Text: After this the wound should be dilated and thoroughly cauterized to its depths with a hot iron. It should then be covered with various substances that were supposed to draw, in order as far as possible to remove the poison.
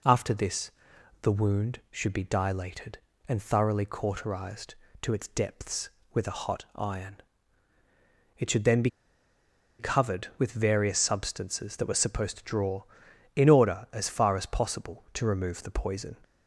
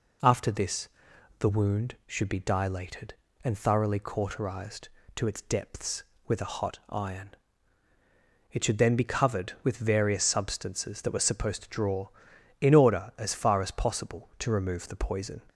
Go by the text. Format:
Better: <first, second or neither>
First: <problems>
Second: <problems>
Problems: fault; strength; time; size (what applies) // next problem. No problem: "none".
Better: second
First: pauses between "this" and "the"; noticeable; at 0.7 s; 0.50 s long // pauses between "be" and "covered"; noticeable; at 8.9 s; 0.88 s long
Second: pauses between "this" and "the"; noticeable; at 0.8 s; 0.50 s long